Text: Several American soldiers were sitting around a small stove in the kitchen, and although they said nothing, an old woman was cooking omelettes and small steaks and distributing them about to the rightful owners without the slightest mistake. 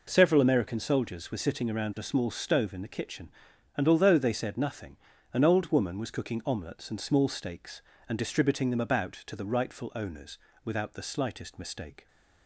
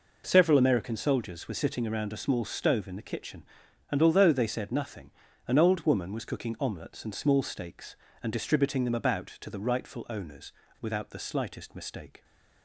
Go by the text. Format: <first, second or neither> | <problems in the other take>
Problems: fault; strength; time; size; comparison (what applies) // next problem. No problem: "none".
neither | pauses between "owners" and "without"; slight; the same in both